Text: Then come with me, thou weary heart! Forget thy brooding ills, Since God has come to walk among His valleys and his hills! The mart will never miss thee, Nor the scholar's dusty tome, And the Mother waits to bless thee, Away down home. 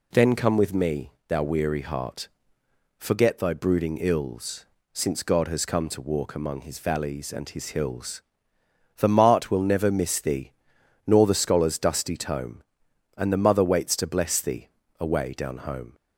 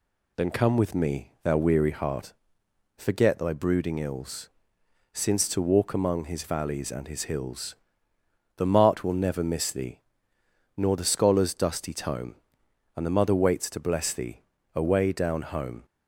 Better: first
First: none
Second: skips "God has come"; at 5.4 s

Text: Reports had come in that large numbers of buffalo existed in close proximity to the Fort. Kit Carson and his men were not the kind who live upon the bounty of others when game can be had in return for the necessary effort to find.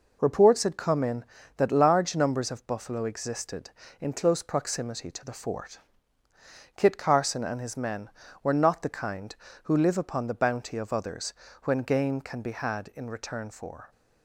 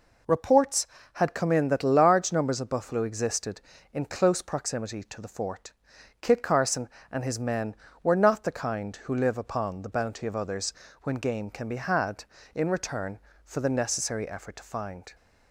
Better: second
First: pauses between "others" and "when"; slight; at 11.3 s; 0.32 s long // stops before "the necessary effort to find"; at 13.9 s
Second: pauses between "others" and "when"; slight; at 10.7 s; 0.30 s long

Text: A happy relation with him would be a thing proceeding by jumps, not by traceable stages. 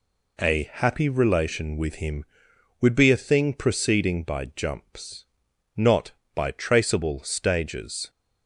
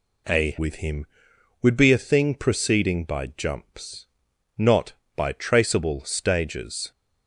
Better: first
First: none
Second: skips "happy relation"; at 0.5 s

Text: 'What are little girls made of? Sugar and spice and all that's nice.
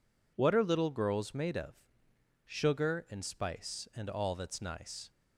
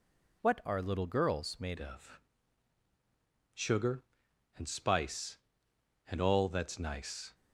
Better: first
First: none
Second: changes voice at "of"; from 1.7 s on; 5.6 s long

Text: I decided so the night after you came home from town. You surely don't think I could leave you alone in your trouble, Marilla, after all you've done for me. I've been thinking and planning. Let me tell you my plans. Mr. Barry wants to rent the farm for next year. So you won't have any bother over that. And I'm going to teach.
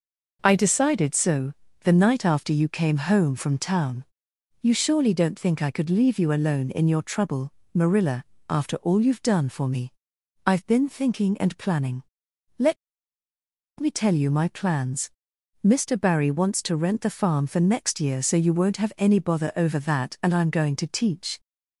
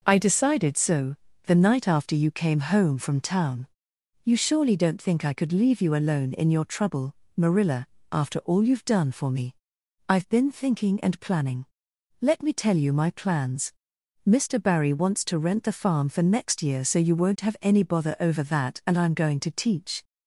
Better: second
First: pauses between "so" and "the"; slight; at 1.5 s; 0.30 s long // pauses between "Let" and "me"; at 12.7 s; 1.0 s long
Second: pauses between "so" and "the"; slight; at 1.1 s; 0.30 s long

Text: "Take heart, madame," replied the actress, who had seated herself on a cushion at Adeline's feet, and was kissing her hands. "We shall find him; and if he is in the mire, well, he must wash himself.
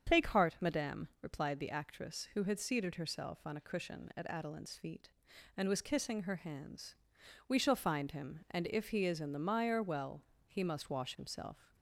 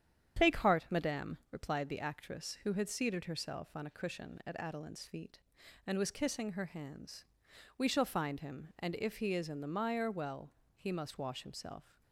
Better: first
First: starts louder than the rest; strong; until 1.2 s; 7.5 dB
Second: gets quieter; noticeable; throughout; 4 dB // starts louder than the rest; strong; until 1.5 s; 9 dB

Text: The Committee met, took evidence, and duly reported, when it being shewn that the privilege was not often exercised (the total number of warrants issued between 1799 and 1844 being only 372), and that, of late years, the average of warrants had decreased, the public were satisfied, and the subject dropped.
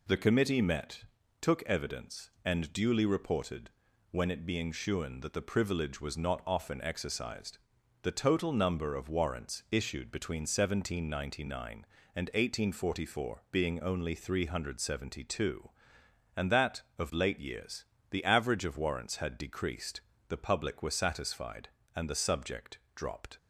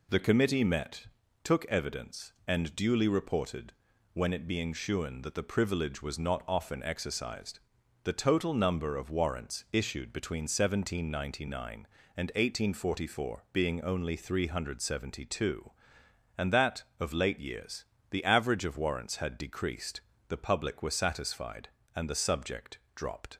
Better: neither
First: pauses between "subject" and "dropped"; slight; at 22.7 s; 0.16 s long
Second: pauses between "subject" and "dropped"; slight; at 22.7 s; 0.16 s long

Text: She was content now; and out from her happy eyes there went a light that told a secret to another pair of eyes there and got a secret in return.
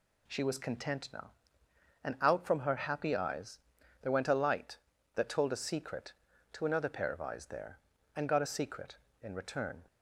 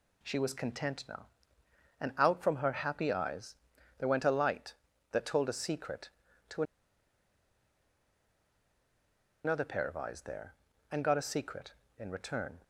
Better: first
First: pauses between "eyes" and "there"; at 3.5 s; 0.44 s long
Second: pauses between "eyes" and "there"; at 3.5 s; 0.44 s long // pauses between "to" and "another"; strong; at 6.6 s; 2.8 s long

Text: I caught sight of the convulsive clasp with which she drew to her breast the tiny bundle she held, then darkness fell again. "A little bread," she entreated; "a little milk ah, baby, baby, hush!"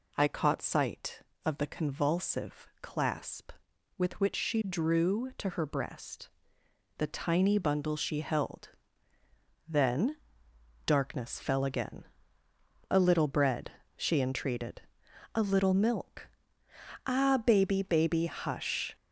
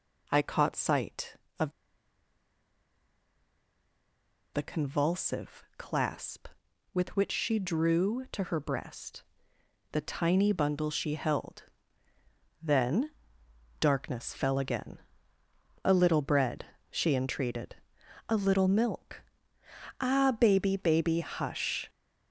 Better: first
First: pauses between "convulsive" and "clasp"; slight; at 2.6 s; 0.16 s long // pauses between "breast" and "the"; noticeable; at 6.2 s; 0.68 s long // pauses between "then" and "darkness"; noticeable; at 10.1 s; 0.70 s long // pauses between "milk" and "ah"; noticeable; at 16.2 s; 0.76 s long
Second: pauses between "of" and "the"; strong; at 1.7 s; 2.8 s long // pauses between "convulsive" and "clasp"; slight; at 5.6 s; 0.16 s long // pauses between "breast" and "the"; noticeable; at 9.2 s; 0.68 s long // pauses between "then" and "darkness"; noticeable; at 13.0 s; 0.70 s long // pauses between "milk" and "ah"; noticeable; at 19.2 s; 0.76 s long

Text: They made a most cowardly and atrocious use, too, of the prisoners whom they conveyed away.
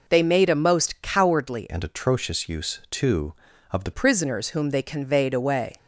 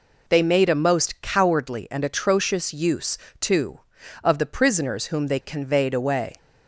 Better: second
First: changes voice from "and" to "the"; from 1.7 to 3.9 s; 2.2 s long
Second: none

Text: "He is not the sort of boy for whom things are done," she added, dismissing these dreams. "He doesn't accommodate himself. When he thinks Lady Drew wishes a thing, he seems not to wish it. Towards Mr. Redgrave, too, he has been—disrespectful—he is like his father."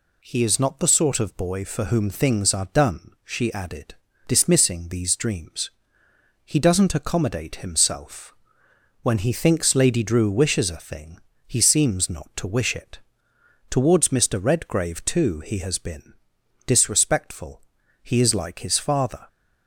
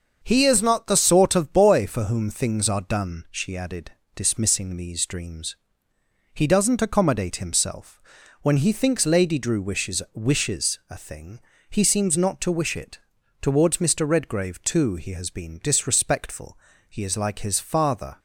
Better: first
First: none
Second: starts louder than the rest; until 1.2 s; 6.5 dB // says "wishes" twice; at 10.1 s

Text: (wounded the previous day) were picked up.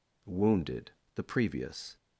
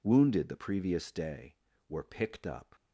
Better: second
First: pauses between "wounded" and "the"; slight; at 0.9 s; 0.24 s long // stops before "day were picked up"; at 1.9 s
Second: none

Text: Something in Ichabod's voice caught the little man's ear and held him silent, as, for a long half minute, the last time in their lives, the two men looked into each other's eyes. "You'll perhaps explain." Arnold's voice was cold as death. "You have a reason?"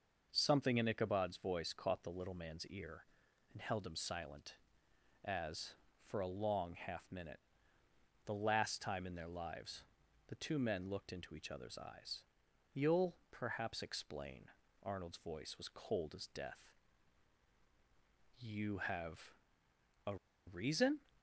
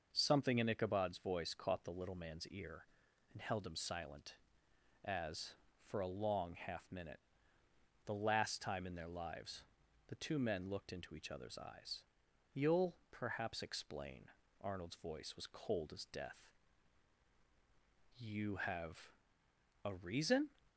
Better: second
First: pauses between "You'll" and "perhaps"; slight; at 13.1 s; 0.16 s long // pauses between "have" and "a"; noticeable; at 19.3 s; 0.72 s long // pauses between "a" and "reason"; slight; at 20.1 s; 0.31 s long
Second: pauses between "You'll" and "perhaps"; slight; at 12.9 s; 0.16 s long // pauses between "have" and "a"; noticeable; at 19.1 s; 0.72 s long

